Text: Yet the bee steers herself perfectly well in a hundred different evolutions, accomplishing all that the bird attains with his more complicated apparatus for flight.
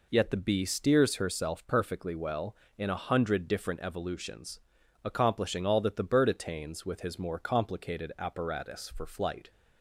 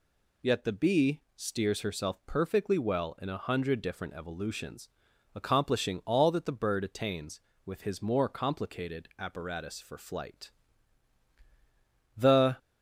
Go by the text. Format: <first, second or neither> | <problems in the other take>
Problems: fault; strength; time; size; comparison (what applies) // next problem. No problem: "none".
first | goes on to say "The"; slight; from 12.1 s on; 0.42 s long